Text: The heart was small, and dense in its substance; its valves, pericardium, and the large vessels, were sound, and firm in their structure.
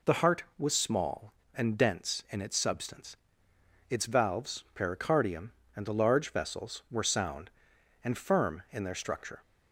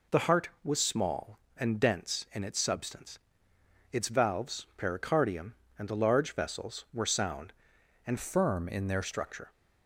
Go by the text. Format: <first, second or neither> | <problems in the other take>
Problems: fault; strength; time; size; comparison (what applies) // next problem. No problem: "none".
first | changes voice from "firm" to "their"; from 8.1 to 9.0 s; 0.9 s long